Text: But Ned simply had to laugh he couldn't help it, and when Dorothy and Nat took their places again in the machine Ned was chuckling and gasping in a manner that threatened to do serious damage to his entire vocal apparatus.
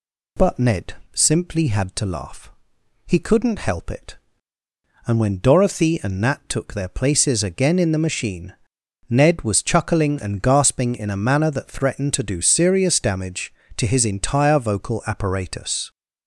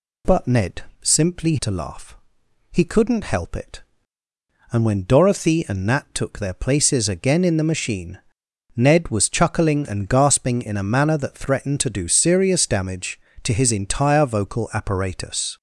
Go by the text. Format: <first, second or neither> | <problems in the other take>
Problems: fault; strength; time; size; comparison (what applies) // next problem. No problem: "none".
first | pauses between "Ned" and "simply"; slight; at 0.8 s; 0.20 s long; slight in the first // skips "had"; at 1.5 s // pauses between "laugh" and "he"; noticeable; at 2.1 s; 0.56 s long; noticeable in the first // pauses between "machine" and "Ned"; noticeable; at 8.1 s; 0.56 s long; noticeable in the first